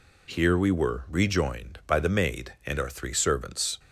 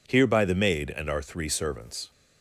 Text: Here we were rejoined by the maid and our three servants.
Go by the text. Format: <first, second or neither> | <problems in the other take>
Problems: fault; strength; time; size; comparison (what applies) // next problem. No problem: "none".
first | skips "we were rejoined"; at 0.2 s